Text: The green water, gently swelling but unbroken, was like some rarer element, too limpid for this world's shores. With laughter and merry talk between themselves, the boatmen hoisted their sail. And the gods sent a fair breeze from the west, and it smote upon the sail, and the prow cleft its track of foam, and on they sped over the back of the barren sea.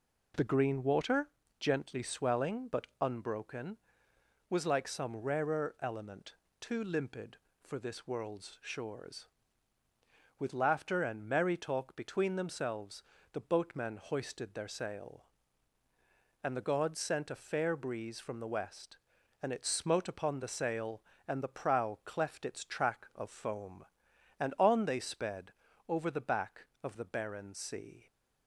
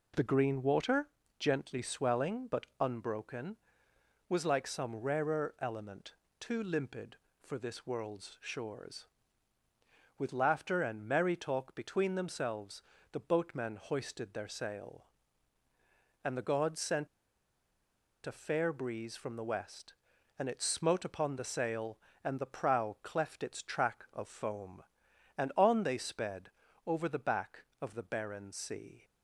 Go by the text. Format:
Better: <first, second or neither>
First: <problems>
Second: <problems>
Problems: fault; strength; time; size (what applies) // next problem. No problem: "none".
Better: first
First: pauses between "sped" and "over"; at 25.5 s; 0.38 s long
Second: pauses between "sent" and "a"; at 17.0 s; 1.1 s long // pauses between "sped" and "over"; at 26.5 s; 0.38 s long